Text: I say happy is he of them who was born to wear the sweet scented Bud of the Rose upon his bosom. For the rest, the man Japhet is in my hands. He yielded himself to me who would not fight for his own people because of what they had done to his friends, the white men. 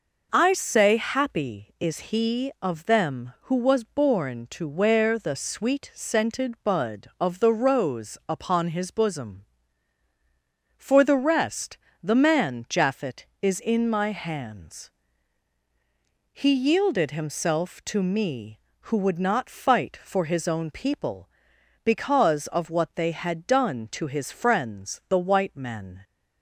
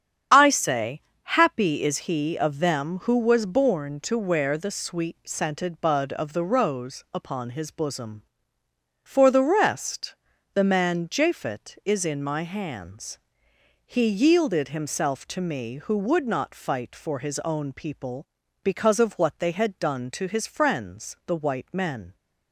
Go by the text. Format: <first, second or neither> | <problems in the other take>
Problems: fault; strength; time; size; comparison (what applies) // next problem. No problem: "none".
first | loses the start of "I"; at 0.3 s; 35 ms // starts louder than the rest; strong; until 1.5 s; 8.5 dB // pauses between "say" and "happy"; slight; at 1.0 s; 0.20 s long